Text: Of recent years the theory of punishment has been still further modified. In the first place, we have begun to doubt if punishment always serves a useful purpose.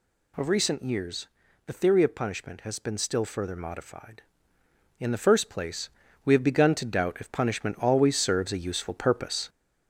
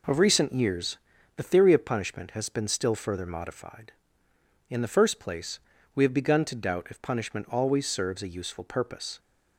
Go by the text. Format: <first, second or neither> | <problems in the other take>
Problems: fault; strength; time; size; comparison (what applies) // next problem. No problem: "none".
second | gets louder; noticeable; throughout; 4.5 dB // pauses between "years" and "the"; slight; at 1.2 s; 0.36 s long; slight in the second